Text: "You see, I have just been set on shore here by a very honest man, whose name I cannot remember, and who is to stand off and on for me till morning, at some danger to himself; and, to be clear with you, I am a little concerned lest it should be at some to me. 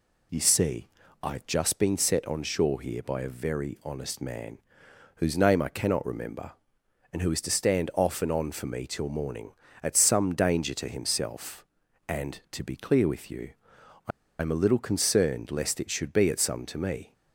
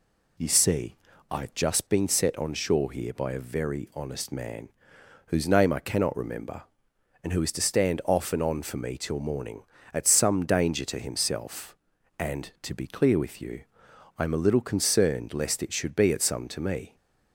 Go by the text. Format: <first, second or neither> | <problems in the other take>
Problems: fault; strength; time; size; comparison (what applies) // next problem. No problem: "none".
second | pauses between "I" and "am"; slight; at 14.1 s; 0.29 s long